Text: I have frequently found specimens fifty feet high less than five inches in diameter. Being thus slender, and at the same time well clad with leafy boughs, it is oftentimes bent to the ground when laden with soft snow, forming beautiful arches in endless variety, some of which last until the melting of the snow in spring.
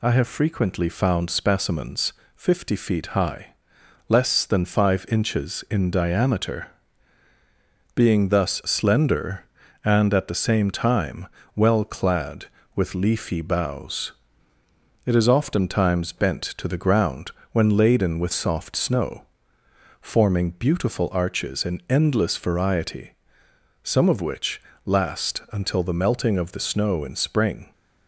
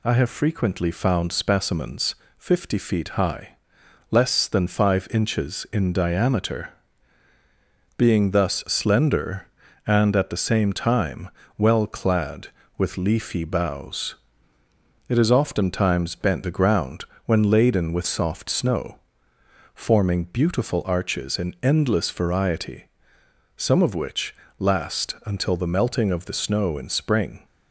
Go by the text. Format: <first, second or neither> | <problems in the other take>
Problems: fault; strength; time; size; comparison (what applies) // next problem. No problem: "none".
first | pauses between "specimens" and "fifty"; slight; at 2.1 s; 0.22 s long; slight in the first // pauses between "high" and "less"; noticeable; at 3.5 s; 0.54 s long; noticeable in the first // pauses between "time" and "well"; slight; at 11.2 s; 0.30 s long; slight in the first // skips "to"; at 16.4 s // pauses between "ground" and "when"; slight; at 17.0 s; 0.20 s long; slight in the first // pauses between "which" and "last"; slight; at 24.3 s; 0.24 s long; slight in the first